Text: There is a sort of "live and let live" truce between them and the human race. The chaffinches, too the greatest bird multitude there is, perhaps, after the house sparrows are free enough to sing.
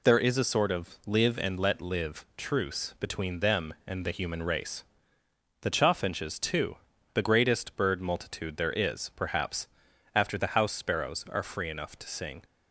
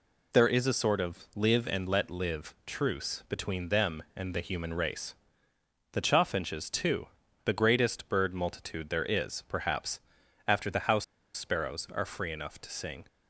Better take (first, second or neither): first